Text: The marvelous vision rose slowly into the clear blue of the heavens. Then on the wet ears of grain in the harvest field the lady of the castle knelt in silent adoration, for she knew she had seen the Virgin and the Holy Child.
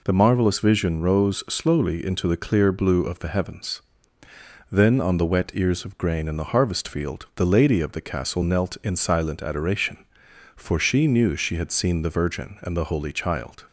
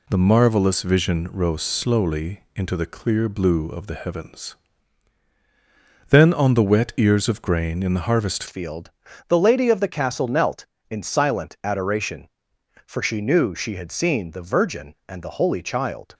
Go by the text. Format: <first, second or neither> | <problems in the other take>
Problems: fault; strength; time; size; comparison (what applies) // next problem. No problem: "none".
first | changes voice at "field"; from 8.4 s on; 7.7 s long // pauses between "field" and "the"; slight; at 8.9 s; 0.34 s long